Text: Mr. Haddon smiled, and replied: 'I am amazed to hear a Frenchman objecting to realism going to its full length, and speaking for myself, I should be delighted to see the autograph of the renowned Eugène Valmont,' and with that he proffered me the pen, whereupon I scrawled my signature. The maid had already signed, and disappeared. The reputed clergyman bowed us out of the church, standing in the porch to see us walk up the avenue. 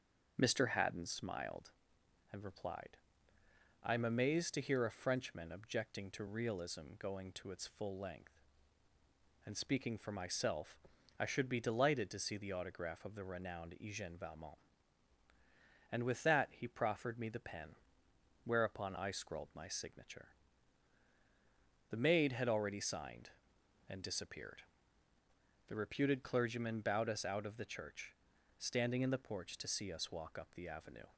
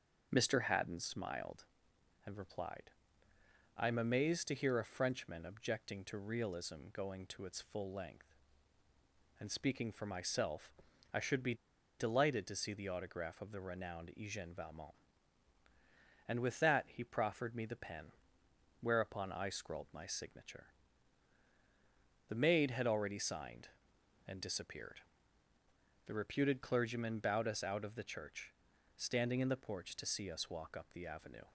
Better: first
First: starts louder than the rest; until 1.3 s; 6.5 dB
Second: starts louder than the rest; until 1.3 s; 7 dB // pauses between "be" and "delighted"; at 11.5 s; 0.44 s long

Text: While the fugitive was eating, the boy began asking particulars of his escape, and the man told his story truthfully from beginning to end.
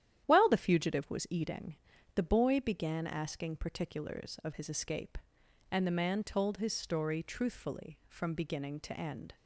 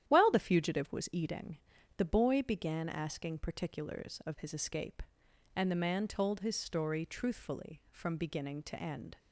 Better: neither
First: starts louder than the rest; strong; until 1.2 s; 11 dB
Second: starts louder than the rest; strong; until 1.0 s; 11 dB

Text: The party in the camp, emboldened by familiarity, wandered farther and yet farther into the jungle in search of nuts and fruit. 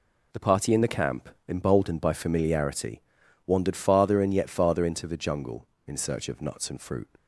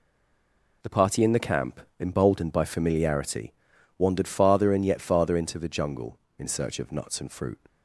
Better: first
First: none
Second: stays silent before the first word; slight; until 0.8 s; 0.8 s long

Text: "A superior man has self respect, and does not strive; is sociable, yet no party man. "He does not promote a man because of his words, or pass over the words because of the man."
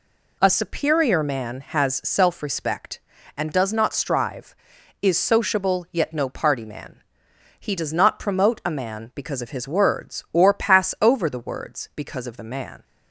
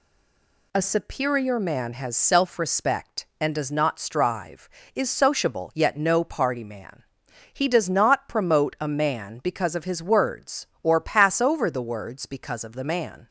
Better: first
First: none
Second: stays silent before the first word; slight; until 0.7 s; 0.7 s long

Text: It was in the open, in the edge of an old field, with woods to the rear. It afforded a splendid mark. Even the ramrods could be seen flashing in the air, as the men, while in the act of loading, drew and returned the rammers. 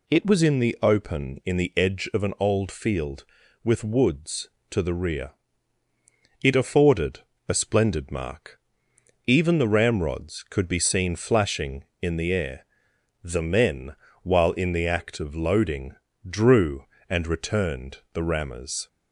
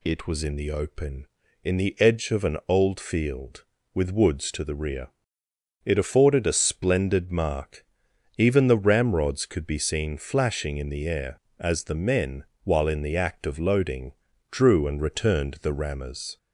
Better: second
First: pauses between "afforded" and "a"; slight; at 7.2 s; 0.26 s long // skips "as"; at 12.9 s // pauses between "returned" and "the"; slight; at 17.9 s; 0.16 s long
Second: none

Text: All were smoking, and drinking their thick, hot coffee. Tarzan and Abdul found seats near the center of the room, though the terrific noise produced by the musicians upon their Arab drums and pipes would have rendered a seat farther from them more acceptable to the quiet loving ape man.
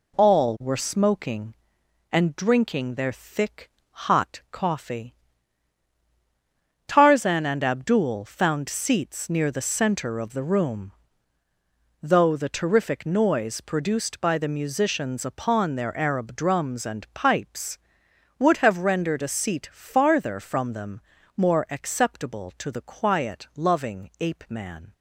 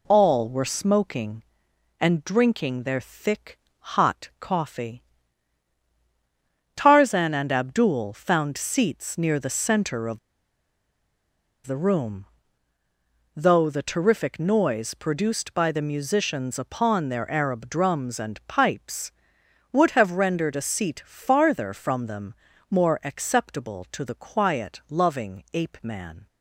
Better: first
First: pauses between "them" and "more"; slight; at 21.0 s; 0.36 s long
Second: pauses between "of" and "the"; strong; at 10.1 s; 1.4 s long // pauses between "them" and "more"; slight; at 22.3 s; 0.36 s long

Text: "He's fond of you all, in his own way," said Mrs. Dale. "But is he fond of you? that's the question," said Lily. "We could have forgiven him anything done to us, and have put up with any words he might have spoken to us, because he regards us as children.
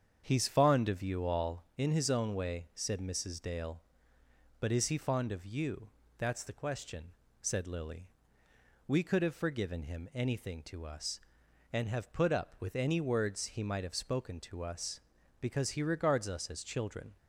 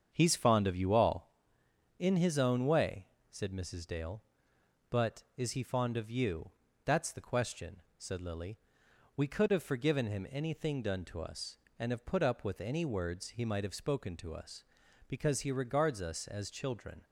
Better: second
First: starts louder than the rest; strong; until 1.2 s; 7.5 dB // skips "done"; at 10.6 s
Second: starts louder than the rest; strong; until 1.1 s; 7.5 dB

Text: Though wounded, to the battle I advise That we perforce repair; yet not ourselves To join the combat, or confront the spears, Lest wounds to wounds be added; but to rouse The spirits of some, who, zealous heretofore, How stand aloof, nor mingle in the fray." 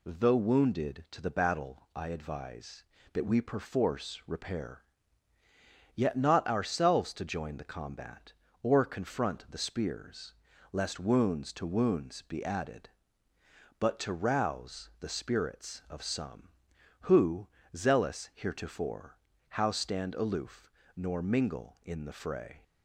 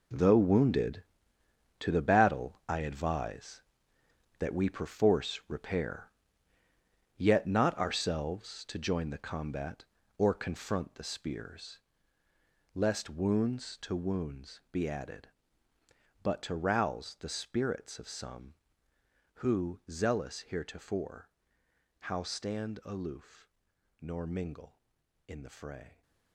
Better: first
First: none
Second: gets quieter; strong; throughout; 11.5 dB

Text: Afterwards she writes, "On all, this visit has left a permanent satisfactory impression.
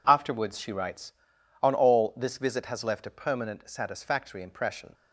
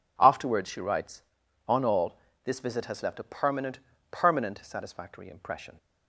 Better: first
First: none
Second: says "permanent" twice; at 4.1 s

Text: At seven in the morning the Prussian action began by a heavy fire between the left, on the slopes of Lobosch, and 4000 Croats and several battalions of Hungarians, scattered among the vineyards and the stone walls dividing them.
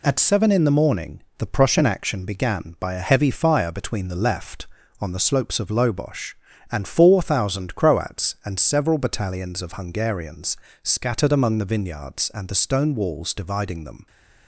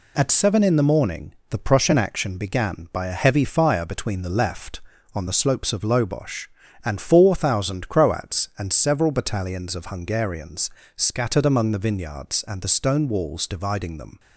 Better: neither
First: pauses between "morning" and "the"; slight; at 1.2 s; 0.16 s long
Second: pauses between "morning" and "the"; slight; at 1.3 s; 0.16 s long

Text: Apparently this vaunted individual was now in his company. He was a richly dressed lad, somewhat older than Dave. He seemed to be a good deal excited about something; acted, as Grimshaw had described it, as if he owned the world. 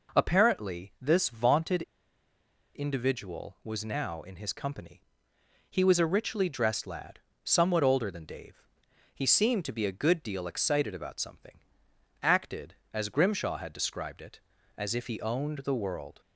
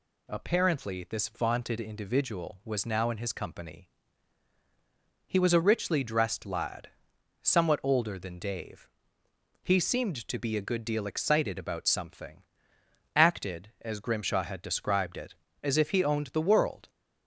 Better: second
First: pauses between "vaunted" and "individual"; noticeable; at 1.8 s; 0.93 s long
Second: none

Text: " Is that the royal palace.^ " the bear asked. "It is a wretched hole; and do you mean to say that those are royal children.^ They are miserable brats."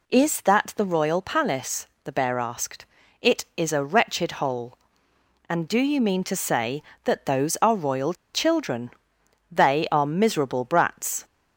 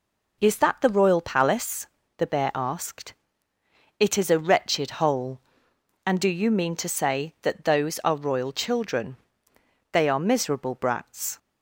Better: second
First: pauses between "royal" and "children"; slight; at 8.1 s; 0.20 s long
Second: none

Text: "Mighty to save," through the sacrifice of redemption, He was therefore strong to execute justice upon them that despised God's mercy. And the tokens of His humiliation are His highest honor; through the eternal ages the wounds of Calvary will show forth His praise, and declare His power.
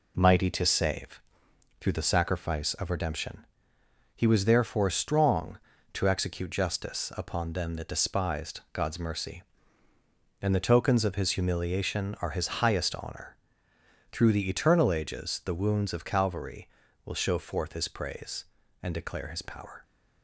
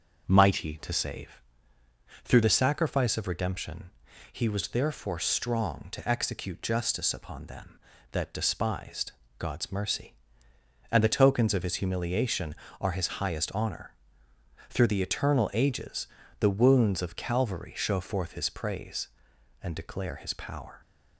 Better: first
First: none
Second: starts louder than the rest; until 1.2 s; 6.5 dB // pauses between "despised" and "God's"; slight; at 9.1 s; 0.26 s long // pauses between "ages" and "the"; slight; at 16.0 s; 0.32 s long // skips "will"; at 17.7 s

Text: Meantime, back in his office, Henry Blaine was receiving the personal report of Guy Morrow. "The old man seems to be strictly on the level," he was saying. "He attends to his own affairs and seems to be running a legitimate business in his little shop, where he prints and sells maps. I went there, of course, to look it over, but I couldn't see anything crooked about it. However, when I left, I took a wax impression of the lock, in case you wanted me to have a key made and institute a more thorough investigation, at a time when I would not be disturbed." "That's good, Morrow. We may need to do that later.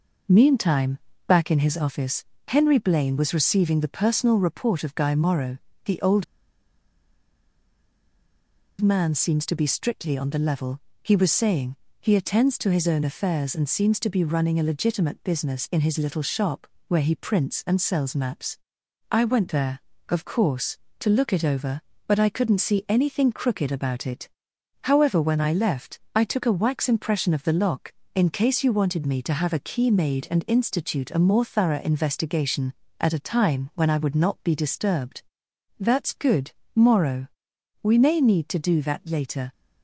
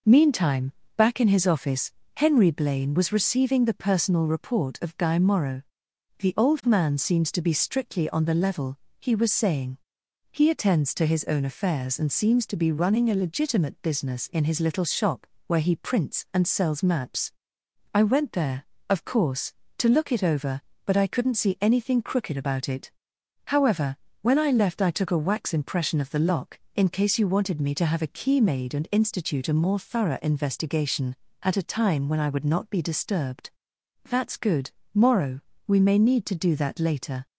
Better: second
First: pauses between "old" and "man"; strong; at 6.2 s; 2.5 s long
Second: none

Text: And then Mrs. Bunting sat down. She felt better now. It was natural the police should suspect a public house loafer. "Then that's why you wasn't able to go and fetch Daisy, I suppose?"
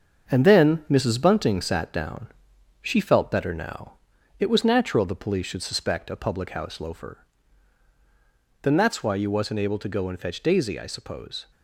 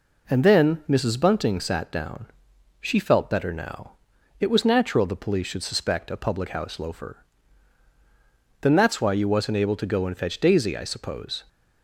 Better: second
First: gets quieter; noticeable; throughout; 6 dB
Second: none

